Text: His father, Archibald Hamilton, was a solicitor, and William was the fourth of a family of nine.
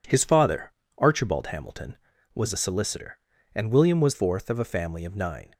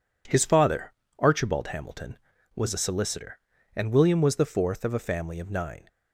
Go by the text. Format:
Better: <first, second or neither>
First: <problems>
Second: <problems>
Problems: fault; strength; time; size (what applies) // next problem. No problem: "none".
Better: second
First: skips "the"; at 4.1 s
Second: none